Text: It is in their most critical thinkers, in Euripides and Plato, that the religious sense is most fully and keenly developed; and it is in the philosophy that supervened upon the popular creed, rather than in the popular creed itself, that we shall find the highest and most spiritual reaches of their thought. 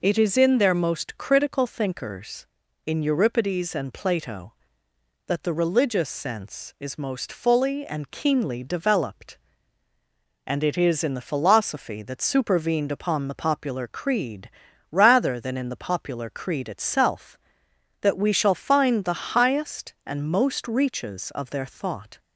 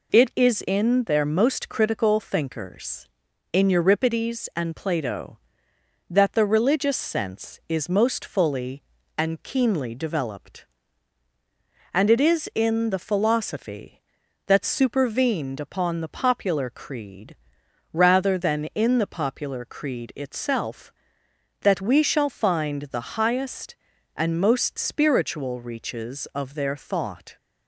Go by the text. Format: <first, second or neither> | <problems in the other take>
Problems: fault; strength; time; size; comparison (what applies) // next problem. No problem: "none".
second | skips "spiritual"; at 20.6 s